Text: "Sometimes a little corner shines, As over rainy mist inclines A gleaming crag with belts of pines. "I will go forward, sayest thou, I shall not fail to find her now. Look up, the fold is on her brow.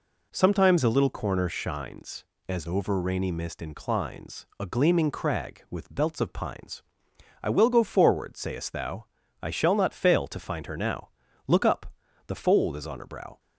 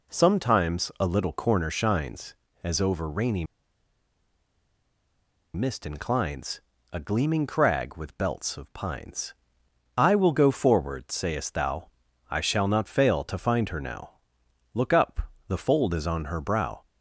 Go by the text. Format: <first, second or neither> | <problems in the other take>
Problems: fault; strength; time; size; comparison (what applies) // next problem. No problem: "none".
first | pauses between "rainy" and "mist"; strong; at 3.4 s; 2.0 s long // pauses between "inclines" and "A"; slight; at 6.6 s; 0.30 s long